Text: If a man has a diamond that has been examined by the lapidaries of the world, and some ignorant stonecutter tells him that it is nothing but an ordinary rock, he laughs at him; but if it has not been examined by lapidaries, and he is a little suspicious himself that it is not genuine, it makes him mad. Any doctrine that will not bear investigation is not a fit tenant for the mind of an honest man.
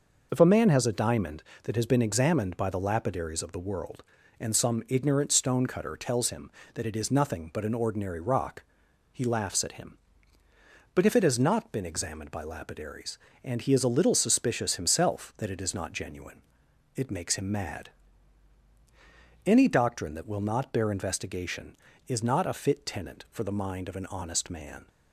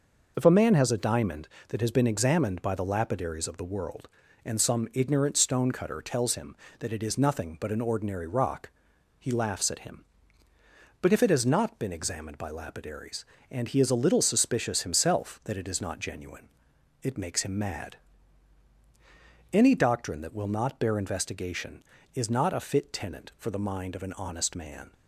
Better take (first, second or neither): neither